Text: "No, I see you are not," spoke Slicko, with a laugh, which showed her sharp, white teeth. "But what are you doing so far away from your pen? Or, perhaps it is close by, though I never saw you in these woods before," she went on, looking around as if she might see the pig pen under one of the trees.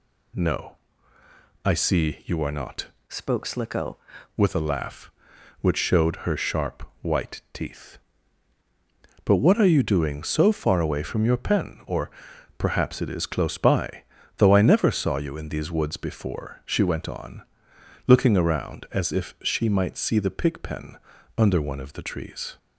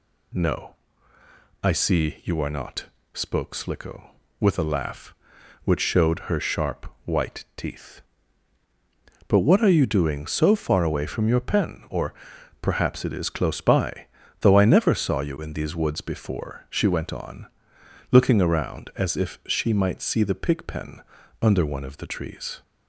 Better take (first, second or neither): second